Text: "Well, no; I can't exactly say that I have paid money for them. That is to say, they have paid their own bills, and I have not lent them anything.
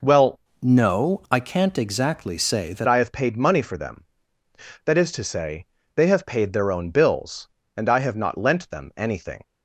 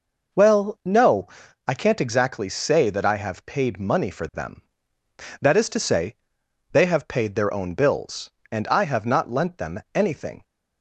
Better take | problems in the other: second | changes voice from "no" to "that"; from 0.6 to 2.8 s; 2.2 s long

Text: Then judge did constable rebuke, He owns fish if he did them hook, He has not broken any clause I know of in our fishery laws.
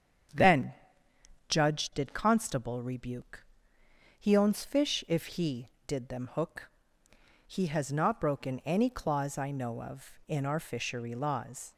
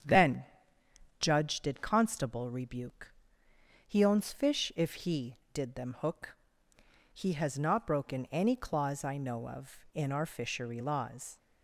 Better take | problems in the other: neither | starts louder than the rest; strong; the same in both // pauses between "Then" and "judge"; noticeable; the same in both

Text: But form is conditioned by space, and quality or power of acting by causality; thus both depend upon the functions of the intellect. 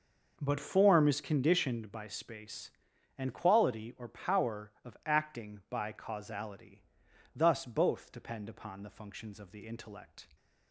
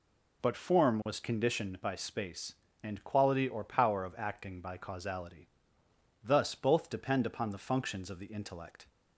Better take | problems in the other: first | says "was" for "is"; at 1.0 s

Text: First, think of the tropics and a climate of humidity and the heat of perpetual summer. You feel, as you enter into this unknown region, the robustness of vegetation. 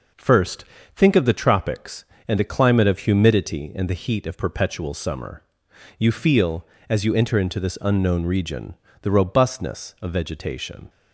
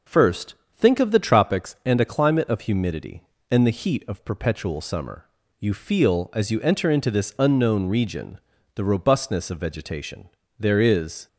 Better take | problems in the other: first | goes on to say "There is"; noticeable; from 10.5 s on; 0.70 s long

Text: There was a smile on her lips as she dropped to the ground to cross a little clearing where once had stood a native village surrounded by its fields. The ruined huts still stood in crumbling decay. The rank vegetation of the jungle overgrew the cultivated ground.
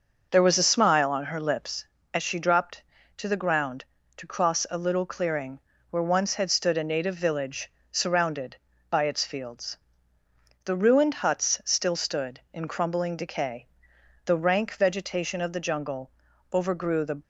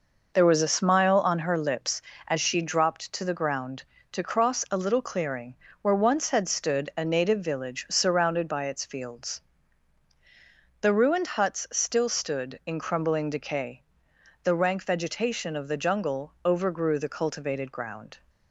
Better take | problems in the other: second | pauses between "clearing" and "where"; slight; at 5.5 s; 0.30 s long; slight in the second // pauses between "village" and "surrounded"; slight; at 7.7 s; 0.18 s long // pauses between "jungle" and "overgrew"; at 16.1 s; 0.42 s long // stops before "cultivated ground"; at 17.2 s

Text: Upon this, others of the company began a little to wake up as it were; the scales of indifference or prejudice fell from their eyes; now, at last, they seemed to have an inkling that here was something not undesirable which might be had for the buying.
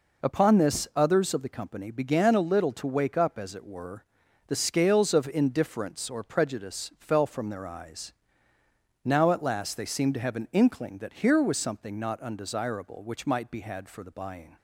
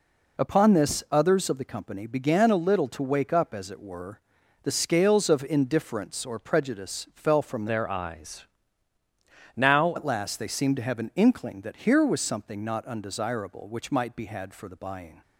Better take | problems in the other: first | changes voice from "their" to "now"; from 7.6 to 9.9 s; 2.3 s long

